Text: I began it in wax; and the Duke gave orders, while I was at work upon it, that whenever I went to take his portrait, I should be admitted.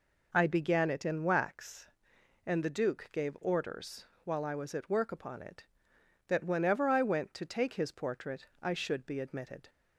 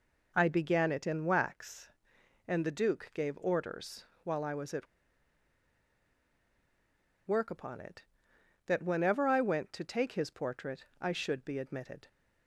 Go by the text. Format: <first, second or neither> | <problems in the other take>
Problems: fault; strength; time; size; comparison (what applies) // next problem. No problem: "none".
first | pauses between "at" and "work"; strong; at 4.8 s; 2.4 s long